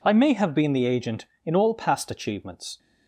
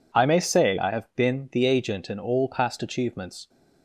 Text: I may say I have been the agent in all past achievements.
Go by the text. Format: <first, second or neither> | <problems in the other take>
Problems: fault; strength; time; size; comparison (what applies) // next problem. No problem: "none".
second | skips "say I"; at 0.3 s